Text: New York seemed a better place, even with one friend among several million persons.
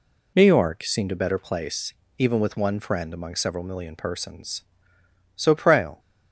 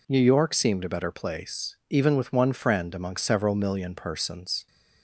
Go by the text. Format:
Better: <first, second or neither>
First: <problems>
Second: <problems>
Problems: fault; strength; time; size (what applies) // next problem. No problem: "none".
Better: second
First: goes on to say "So Prale"; noticeable; from 5.3 s on; 0.64 s long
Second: none